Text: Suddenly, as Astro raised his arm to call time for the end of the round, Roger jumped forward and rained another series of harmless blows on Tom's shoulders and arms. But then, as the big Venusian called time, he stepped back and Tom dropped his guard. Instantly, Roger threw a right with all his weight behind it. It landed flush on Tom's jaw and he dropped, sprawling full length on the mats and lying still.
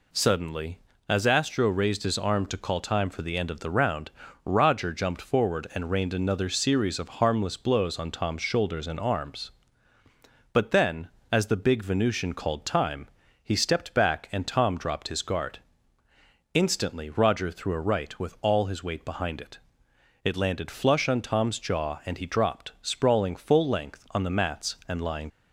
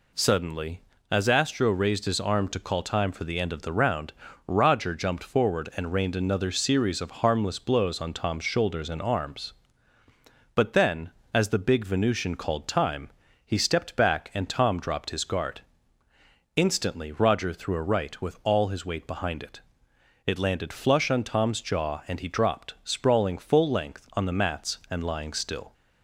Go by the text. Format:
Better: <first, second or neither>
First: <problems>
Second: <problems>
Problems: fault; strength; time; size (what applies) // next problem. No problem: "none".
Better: second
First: stops before "still"; at 25.3 s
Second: none